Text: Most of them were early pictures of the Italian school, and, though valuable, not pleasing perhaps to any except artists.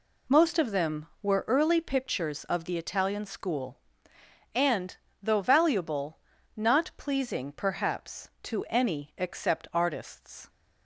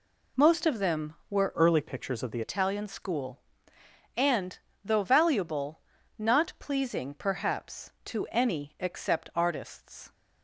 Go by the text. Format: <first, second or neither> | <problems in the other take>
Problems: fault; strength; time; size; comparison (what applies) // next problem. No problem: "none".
first | changes voice from "early" to "the"; from 1.5 to 2.4 s; 0.9 s long